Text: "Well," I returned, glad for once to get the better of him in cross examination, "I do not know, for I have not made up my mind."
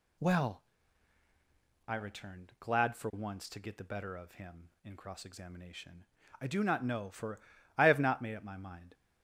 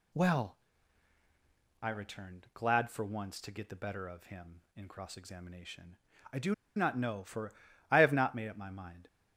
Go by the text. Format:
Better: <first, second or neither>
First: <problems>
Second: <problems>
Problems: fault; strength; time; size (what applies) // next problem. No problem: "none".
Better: first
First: pauses between "for" and "I"; slight; at 7.3 s; 0.36 s long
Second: pauses between "do" and "not"; slight; at 6.5 s; 0.22 s long // pauses between "for" and "I"; slight; at 7.5 s; 0.36 s long